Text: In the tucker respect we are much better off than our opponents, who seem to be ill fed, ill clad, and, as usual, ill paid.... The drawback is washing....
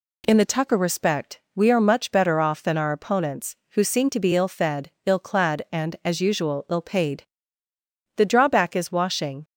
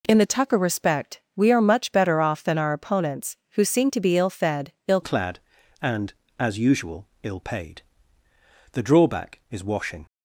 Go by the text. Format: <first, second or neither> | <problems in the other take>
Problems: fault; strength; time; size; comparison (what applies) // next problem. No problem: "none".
first | pauses between "respect" and "we"; slight; at 1.1 s; 0.16 s long; slight in the first // changes voice at "clad"; from 5.0 s on; 5.0 s long